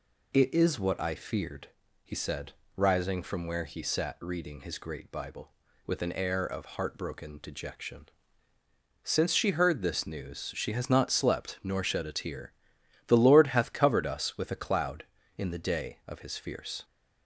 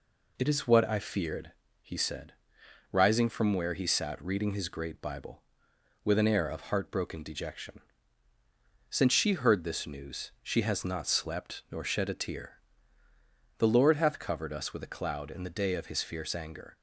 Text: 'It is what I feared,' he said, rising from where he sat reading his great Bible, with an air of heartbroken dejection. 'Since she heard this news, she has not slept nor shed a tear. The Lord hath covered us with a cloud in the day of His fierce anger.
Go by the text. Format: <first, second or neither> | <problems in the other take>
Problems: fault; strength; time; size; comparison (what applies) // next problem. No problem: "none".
second | stops before "anger"; at 16.8 s